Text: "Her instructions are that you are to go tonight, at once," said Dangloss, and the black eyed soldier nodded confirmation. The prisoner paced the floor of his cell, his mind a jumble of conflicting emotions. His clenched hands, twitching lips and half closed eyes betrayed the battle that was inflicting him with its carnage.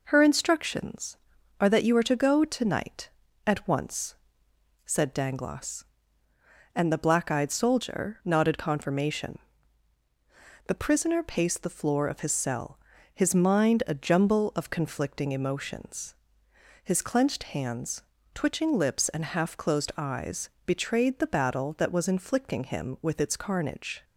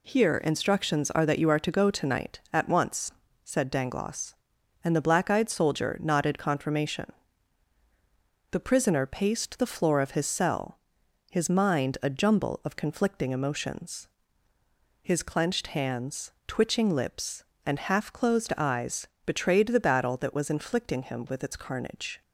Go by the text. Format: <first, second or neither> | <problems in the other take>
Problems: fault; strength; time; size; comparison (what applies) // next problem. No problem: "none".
first | says "Here" for "Her"; at 0.0 s // pauses between "eyes" and "betrayed"; slight; at 19.0 s; 0.18 s long; slight in the first